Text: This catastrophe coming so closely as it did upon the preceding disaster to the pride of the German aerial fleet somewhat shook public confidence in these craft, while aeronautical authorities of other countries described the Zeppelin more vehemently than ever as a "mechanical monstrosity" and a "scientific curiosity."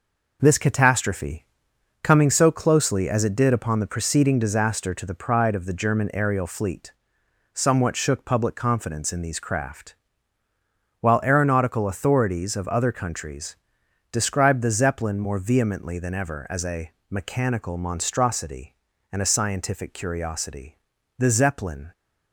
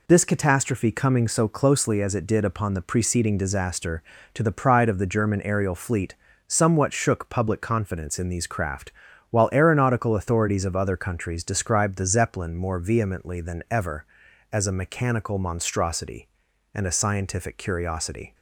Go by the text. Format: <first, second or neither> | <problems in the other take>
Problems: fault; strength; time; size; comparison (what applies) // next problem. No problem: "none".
second | pauses between "catastrophe" and "coming"; noticeable; at 1.4 s; 0.58 s long // pauses between "fleet" and "somewhat"; noticeable; at 6.9 s; 0.59 s long; slight in the second // pauses between "countries" and "described"; noticeable; at 13.5 s; 0.56 s long // pauses between "a" and "mechanical"; slight; at 16.9 s; 0.18 s long // goes on to say "The Zeppelin"; noticeable; from 21.1 s on; 0.74 s long